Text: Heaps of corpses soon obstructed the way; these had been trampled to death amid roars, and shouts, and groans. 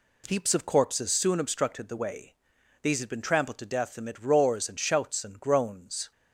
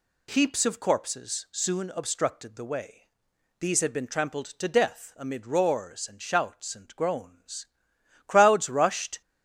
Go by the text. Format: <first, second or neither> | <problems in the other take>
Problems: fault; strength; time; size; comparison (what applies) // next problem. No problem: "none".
first | goes on to say "Crowds rushed"; noticeable; from 8.2 s on; 0.94 s long